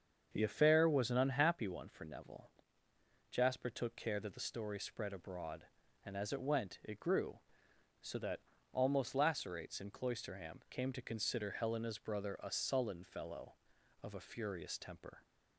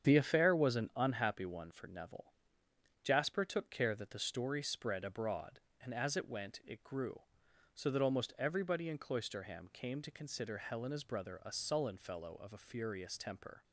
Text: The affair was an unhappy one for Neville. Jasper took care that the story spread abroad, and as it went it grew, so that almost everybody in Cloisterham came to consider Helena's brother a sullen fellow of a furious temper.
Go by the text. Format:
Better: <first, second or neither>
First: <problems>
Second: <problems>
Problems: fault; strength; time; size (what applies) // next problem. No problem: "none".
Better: second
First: starts louder than the rest; until 1.3 s; 7 dB // pauses between "that" and "almost"; slight; at 8.4 s; 0.32 s long // says "lacerates" for "everybody"; at 9.1 s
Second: starts louder than the rest; strong; until 1.1 s; 8 dB